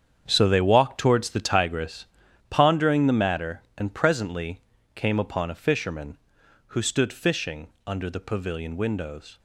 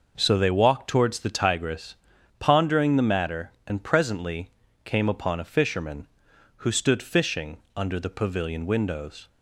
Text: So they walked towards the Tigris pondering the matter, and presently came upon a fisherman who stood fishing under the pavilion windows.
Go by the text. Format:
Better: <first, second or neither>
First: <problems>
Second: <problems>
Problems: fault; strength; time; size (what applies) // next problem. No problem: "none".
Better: second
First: gets quieter; strong; throughout; 12 dB // pauses between "Tigris" and "pondering"; at 2.0 s; 0.44 s long // pauses between "presently" and "came"; slight; at 4.6 s; 0.34 s long // pauses between "fishing" and "under"; slight; at 7.6 s; 0.20 s long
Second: pauses between "Tigris" and "pondering"; at 1.9 s; 0.44 s long // pauses between "presently" and "came"; slight; at 4.4 s; 0.34 s long // pauses between "fishing" and "under"; slight; at 7.5 s; 0.20 s long